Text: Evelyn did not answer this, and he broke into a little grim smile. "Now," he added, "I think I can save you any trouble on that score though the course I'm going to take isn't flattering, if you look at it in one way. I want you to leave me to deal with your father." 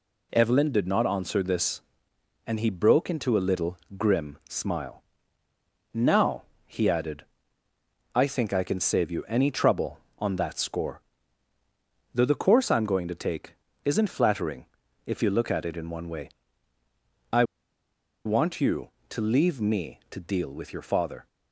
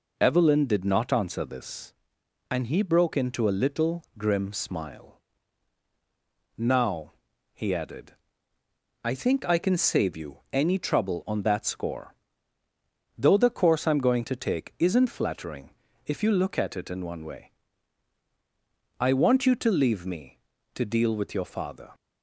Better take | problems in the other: second | pauses between "little" and "grim"; slight; at 3.7 s; 0.20 s long; slight in the second // pauses between "score" and "though"; at 11.0 s; 1.1 s long; also in the second // pauses between "take" and "isn't"; slight; at 13.5 s; 0.32 s long // pauses between "I" and "want"; noticeable; at 17.4 s; 0.81 s long

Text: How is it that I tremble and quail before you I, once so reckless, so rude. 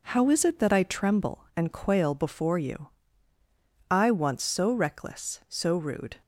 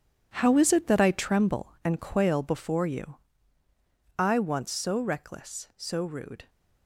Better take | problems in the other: first | gets quieter; strong; throughout; 10.5 dB // pauses between "you" and "I"; at 3.1 s; 1.0 s long; also in the first

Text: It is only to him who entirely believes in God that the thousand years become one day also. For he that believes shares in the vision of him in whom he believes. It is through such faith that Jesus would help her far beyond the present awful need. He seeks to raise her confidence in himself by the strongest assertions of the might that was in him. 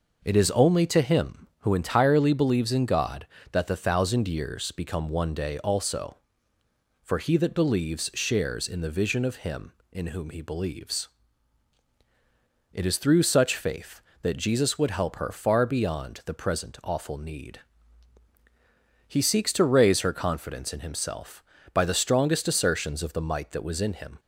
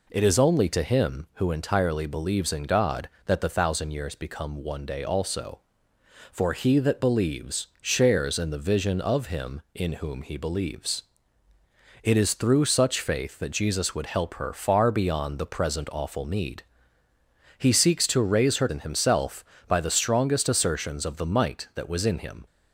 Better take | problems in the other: first | skips "confidence"; at 18.6 s

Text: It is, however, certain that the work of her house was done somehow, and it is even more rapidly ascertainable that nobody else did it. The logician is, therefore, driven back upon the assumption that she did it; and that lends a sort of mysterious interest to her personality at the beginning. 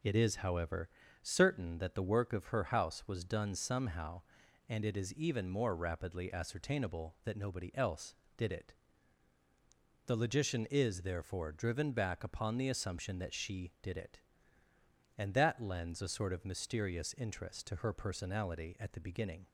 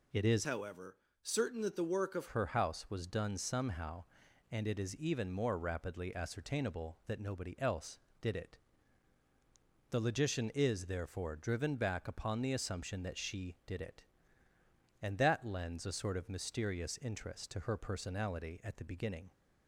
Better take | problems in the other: first | changes voice from "however" to "of"; from 0.4 to 2.2 s; 1.8 s long

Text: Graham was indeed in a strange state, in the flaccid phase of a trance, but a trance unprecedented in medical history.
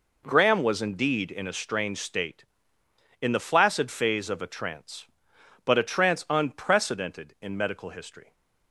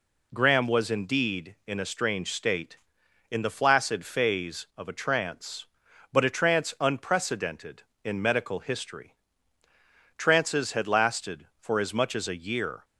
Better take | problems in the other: first | goes on to say "Trances had lasted for as much as a year"; strong; from 10.1 s on; 2.6 s long

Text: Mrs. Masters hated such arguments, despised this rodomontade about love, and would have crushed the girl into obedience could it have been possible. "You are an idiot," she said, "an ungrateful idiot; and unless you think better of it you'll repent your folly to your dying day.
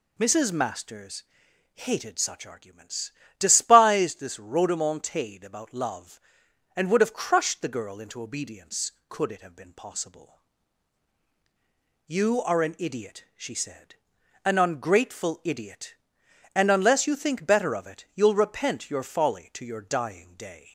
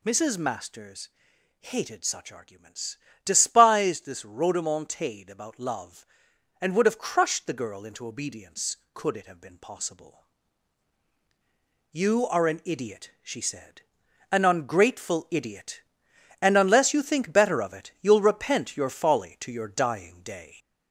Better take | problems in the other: first | gets louder; throughout; 3.5 dB // pauses between "Masters" and "hated"; noticeable; at 1.0 s; 0.52 s long; noticeable in the first

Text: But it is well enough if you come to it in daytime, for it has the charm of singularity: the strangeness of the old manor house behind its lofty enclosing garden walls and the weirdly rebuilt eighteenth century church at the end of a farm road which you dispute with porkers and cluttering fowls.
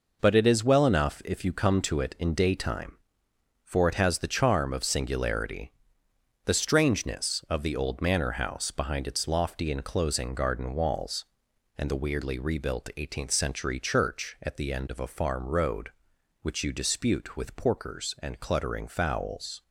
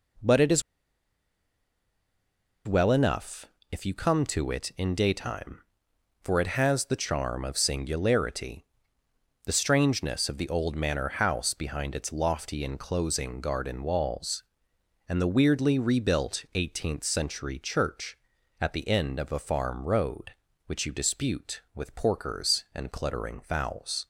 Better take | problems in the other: first | pauses between "is" and "well"; strong; at 0.6 s; 2.0 s long // pauses between "enough" and "if"; slight; at 3.4 s; 0.26 s long

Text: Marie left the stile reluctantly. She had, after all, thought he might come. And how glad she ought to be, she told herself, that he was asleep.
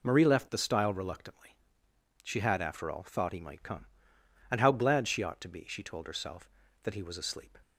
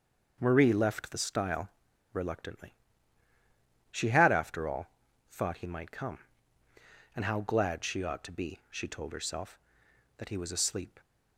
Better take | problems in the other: first | starts louder than the rest; until 1.4 s; 6.5 dB // pauses between "stile" and "reluctantly"; at 1.6 s; 0.45 s long

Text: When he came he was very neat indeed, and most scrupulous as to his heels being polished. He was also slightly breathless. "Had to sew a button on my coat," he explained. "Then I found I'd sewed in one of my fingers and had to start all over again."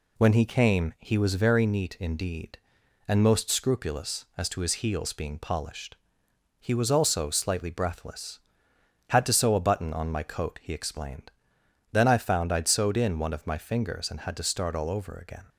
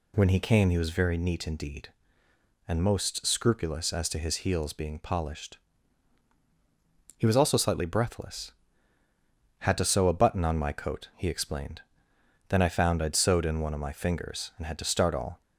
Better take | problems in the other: first | stops before "over again"; at 15.4 s

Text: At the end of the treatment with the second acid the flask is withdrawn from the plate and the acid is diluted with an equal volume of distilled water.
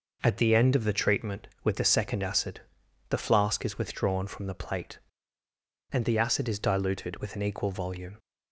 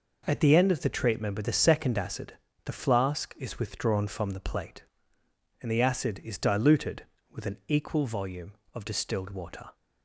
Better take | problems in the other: second | pauses between "acid" and "the"; noticeable; at 2.6 s; 0.48 s long; slight in the second // stops before "of distilled water"; at 8.1 s

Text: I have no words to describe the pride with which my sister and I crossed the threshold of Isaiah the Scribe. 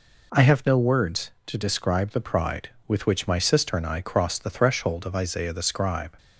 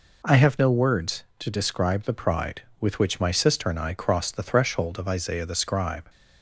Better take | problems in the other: neither | none

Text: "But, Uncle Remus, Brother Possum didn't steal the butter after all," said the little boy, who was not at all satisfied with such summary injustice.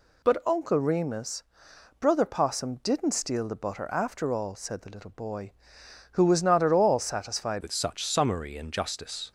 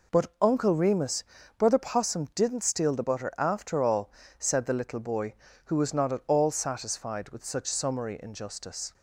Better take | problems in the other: second | changes voice at "with"; from 7.6 s on; 1.7 s long

